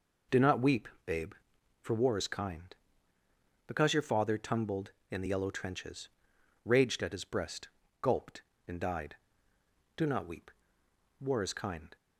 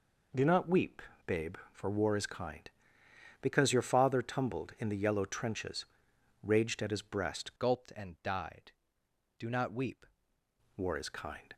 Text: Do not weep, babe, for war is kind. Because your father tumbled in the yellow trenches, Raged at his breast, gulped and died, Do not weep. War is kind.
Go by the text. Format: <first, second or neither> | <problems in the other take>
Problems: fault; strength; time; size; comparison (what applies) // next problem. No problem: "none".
first | changes voice from "gulped" to "weep"; from 7.5 to 10.0 s; 2.5 s long